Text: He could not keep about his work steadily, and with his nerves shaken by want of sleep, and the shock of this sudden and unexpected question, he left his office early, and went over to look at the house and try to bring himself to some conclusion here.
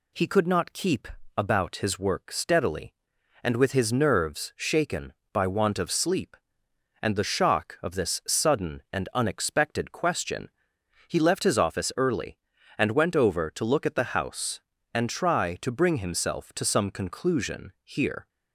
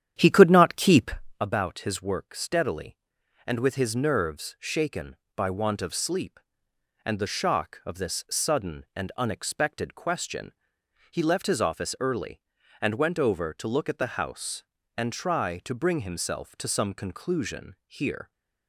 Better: first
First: pauses between "keep" and "about"; slight; at 1.0 s; 0.28 s long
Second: starts louder than the rest; strong; until 1.4 s; 10 dB // pauses between "keep" and "about"; slight; at 1.1 s; 0.28 s long

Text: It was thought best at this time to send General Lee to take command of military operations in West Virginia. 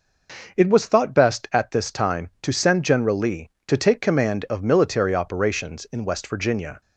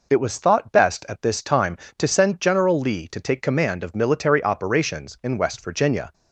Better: neither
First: none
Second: none

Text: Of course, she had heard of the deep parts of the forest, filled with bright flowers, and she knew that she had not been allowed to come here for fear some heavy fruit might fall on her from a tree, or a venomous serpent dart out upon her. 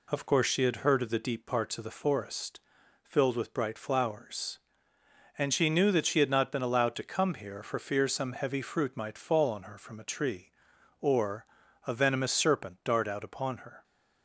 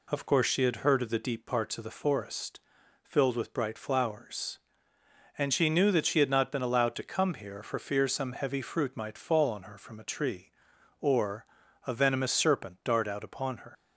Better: first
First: pauses between "or" and "a"; at 11.4 s; 0.42 s long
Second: pauses between "or" and "a"; at 11.4 s; 0.42 s long // leaves "her" unfinished; at 13.7 s; 80 ms

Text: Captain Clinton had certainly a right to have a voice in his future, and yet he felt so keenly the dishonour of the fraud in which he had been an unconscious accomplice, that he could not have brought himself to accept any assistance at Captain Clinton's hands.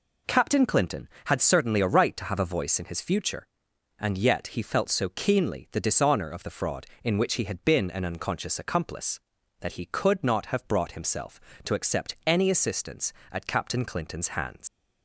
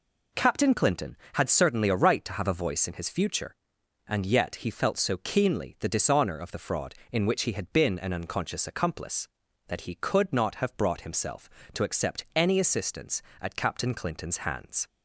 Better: second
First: leaves "hands" unfinished; at 14.6 s; 110 ms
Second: none

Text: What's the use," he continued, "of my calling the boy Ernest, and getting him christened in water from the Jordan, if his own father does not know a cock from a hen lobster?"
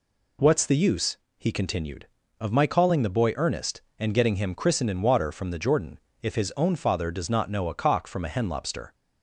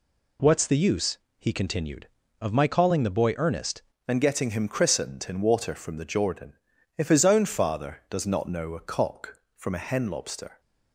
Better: first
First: none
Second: changes voice at "and"; from 4.0 s on; 6.5 s long

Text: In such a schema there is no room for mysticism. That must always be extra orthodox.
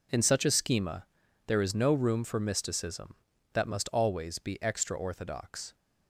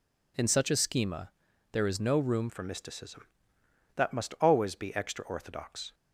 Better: first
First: pauses between "schema" and "there"; at 1.0 s; 0.40 s long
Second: pauses between "schema" and "there"; at 1.3 s; 0.40 s long // changes voice at "for"; from 2.4 s on; 3.5 s long

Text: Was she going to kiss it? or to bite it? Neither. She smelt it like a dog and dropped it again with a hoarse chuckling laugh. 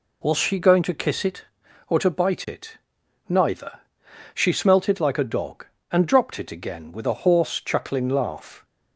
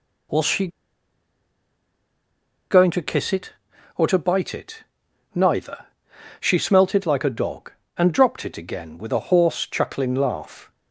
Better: first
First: none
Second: pauses between "she" and "going"; strong; at 0.6 s; 2.0 s long

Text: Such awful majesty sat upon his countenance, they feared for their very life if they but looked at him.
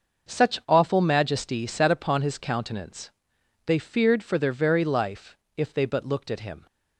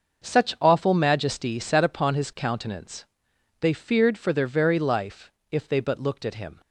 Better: neither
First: starts louder than the rest; noticeable; until 1.3 s; 6 dB // pauses between "life" and "if"; slight; at 5.3 s; 0.20 s long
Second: starts louder than the rest; noticeable; until 1.3 s; 6 dB // pauses between "life" and "if"; slight; at 5.3 s; 0.20 s long

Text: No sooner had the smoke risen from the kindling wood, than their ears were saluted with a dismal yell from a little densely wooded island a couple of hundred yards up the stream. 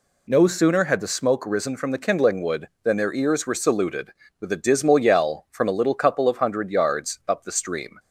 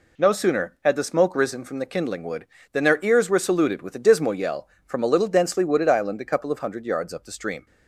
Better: second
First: skips "densely wooded island a"; at 5.9 s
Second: none

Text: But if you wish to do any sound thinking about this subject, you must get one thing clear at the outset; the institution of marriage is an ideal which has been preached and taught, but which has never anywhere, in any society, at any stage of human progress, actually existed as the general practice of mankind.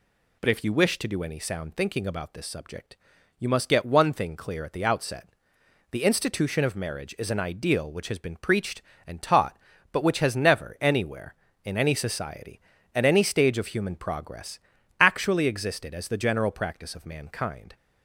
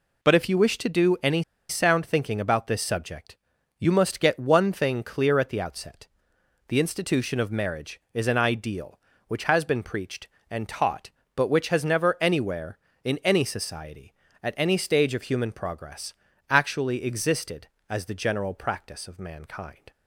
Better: first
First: none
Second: pauses between "any" and "sound"; slight; at 1.4 s; 0.28 s long

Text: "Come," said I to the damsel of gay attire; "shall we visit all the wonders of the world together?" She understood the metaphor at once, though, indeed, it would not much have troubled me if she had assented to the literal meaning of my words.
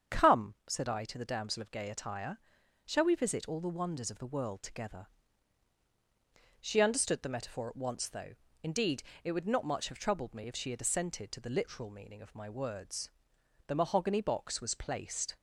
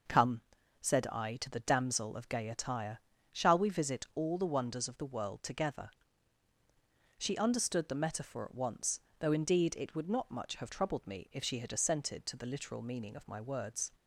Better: second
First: starts louder than the rest; strong; until 1.2 s; 7.5 dB // goes on to say "The mahogany box was placed"; strong; from 13.6 s on; 1.7 s long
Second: none

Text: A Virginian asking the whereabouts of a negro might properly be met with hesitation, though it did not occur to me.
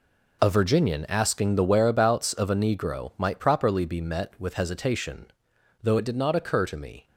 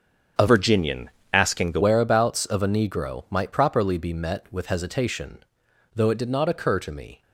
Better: first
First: none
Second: starts louder than the rest; strong; until 1.6 s; 7 dB // changes voice from "Virginian" to "the"; from 0.4 to 1.8 s; 1.4 s long // pauses between "Virginian" and "asking"; slight; at 1.1 s; 0.22 s long

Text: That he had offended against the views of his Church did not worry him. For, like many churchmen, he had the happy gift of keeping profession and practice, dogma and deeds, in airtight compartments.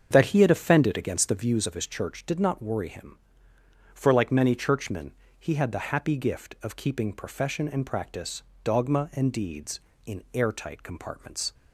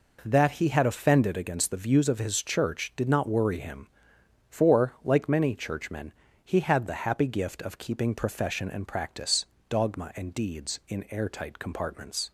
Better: second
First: starts louder than the rest; until 1.4 s; 7 dB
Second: none

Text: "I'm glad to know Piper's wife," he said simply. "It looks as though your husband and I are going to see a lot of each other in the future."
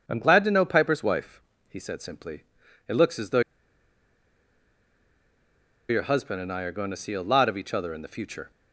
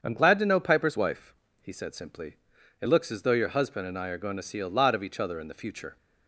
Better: second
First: starts louder than the rest; strong; until 1.0 s; 7 dB // pauses between "though" and "your"; strong; at 3.3 s; 2.4 s long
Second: starts louder than the rest; strong; until 1.0 s; 7 dB

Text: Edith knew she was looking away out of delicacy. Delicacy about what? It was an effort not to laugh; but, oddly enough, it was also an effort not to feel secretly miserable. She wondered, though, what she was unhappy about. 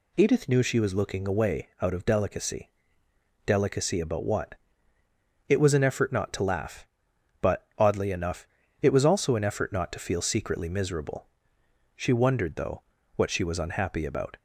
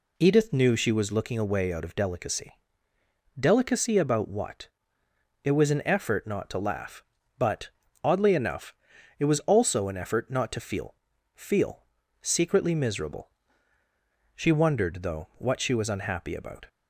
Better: first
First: none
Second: says "feel" twice; at 11.3 s

